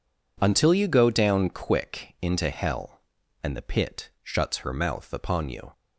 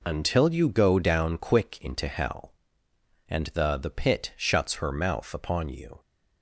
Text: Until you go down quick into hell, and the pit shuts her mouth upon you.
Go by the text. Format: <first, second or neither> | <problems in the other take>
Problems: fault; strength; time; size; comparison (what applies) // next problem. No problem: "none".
first | says "the" twice; at 3.7 s